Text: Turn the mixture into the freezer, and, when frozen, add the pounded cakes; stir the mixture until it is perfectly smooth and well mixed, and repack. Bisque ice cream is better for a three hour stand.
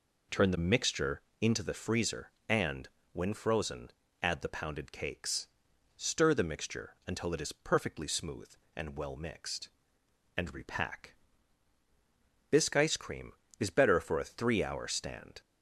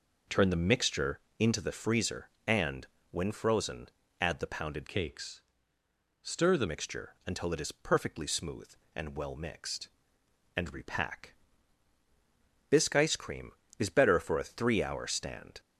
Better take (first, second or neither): first